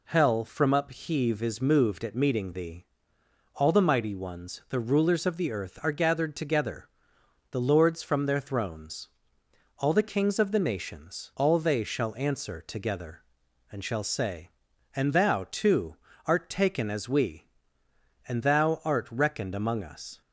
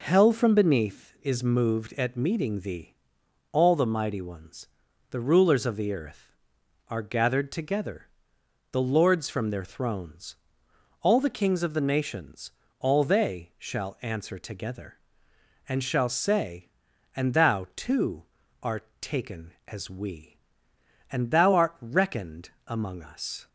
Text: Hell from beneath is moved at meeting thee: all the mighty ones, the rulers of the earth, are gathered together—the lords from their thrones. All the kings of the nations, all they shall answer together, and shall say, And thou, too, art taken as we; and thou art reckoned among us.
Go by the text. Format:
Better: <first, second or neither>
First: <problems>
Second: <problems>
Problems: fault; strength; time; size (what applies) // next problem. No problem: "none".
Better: second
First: says "upheave" for "beneath"; at 0.7 s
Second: none